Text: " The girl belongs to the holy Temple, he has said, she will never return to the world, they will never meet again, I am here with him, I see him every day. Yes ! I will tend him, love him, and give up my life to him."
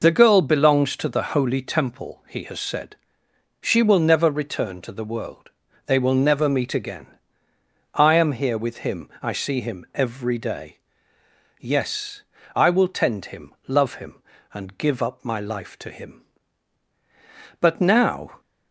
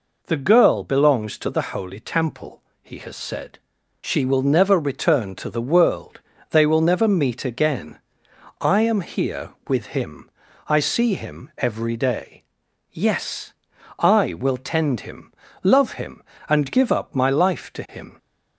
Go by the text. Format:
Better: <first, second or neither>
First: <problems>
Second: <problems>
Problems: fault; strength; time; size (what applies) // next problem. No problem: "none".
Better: second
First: goes on to say "But now"; noticeable; from 17.5 s on; 0.80 s long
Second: none